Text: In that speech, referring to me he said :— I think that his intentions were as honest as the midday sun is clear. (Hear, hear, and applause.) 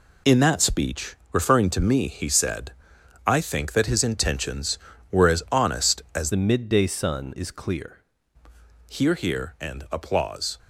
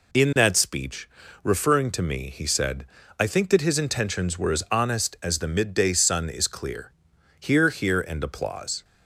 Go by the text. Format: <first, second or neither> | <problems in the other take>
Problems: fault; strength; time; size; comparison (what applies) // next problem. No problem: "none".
second | changes voice from "the" to "clear"; from 6.3 to 8.0 s; 1.7 s long